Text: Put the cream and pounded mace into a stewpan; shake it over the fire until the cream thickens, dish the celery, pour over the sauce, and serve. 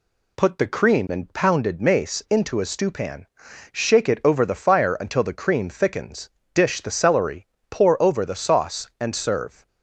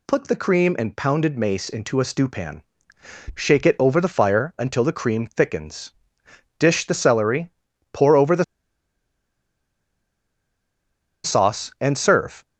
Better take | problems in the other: first | pauses between "the" and "sauce"; strong; at 8.4 s; 2.8 s long

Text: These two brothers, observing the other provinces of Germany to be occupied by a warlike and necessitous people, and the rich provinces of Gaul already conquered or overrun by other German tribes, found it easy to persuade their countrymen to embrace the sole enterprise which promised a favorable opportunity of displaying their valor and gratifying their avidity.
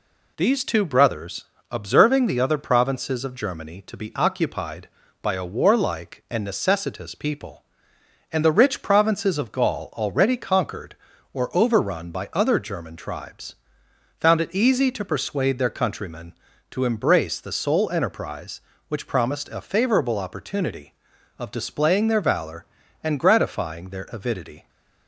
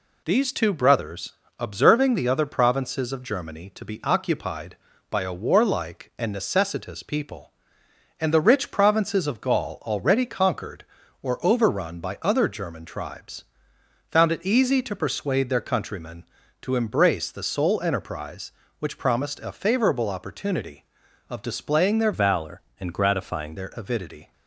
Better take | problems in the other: first | changes voice from "valor" to "gratifying"; from 22.1 to 23.5 s; 1.4 s long

